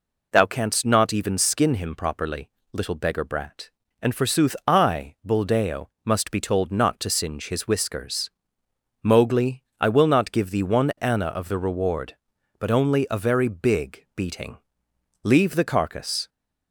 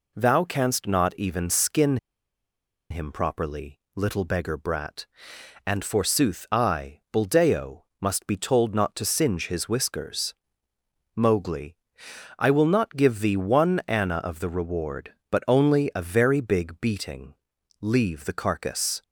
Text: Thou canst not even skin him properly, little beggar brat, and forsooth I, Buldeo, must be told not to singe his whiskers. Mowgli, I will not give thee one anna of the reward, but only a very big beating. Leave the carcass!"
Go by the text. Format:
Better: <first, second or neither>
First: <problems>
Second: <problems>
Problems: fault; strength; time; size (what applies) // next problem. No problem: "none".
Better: first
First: none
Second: pauses between "skin" and "him"; noticeable; at 1.9 s; 0.93 s long